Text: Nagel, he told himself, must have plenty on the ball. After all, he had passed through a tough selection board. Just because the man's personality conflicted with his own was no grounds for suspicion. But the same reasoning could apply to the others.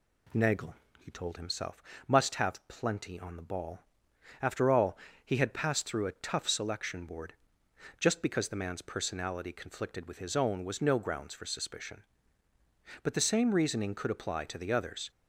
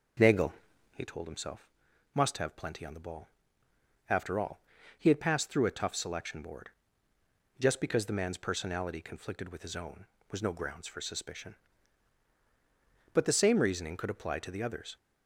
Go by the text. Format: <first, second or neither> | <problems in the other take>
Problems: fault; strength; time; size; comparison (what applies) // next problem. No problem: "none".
first | starts louder than the rest; noticeable; until 1.2 s; 5.5 dB